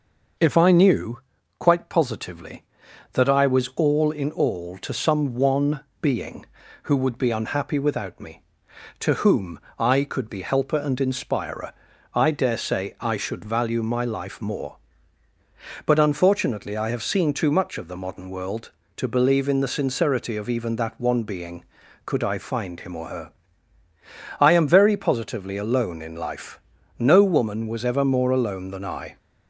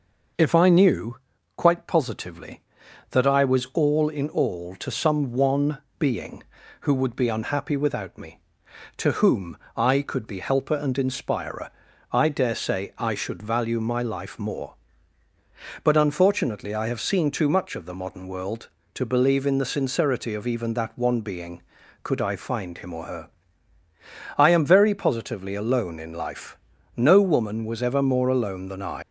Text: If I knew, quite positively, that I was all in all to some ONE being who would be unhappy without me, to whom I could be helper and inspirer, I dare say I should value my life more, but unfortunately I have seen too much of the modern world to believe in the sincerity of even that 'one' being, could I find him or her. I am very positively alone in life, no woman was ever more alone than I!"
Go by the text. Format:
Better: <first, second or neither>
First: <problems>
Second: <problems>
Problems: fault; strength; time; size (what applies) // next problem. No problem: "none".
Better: first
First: pauses between "ONE" and "being"; slight; at 5.7 s; 0.20 s long // pauses between "whom" and "I"; slight; at 9.5 s; 0.20 s long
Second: pauses between "ONE" and "being"; slight; at 5.7 s; 0.20 s long // pauses between "whom" and "I"; slight; at 9.5 s; 0.20 s long // leaves "I" unfinished; at 29.0 s; 125 ms